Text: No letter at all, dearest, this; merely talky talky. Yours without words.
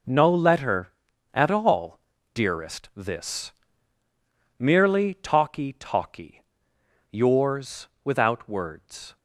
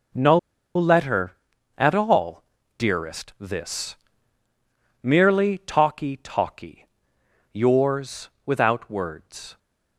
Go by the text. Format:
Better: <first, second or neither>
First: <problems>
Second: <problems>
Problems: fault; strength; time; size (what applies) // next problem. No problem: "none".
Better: first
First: pauses between "Yours" and "without"; slight; at 7.8 s; 0.16 s long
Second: pauses between "No" and "letter"; at 0.3 s; 0.37 s long // pauses between "Yours" and "without"; slight; at 8.2 s; 0.16 s long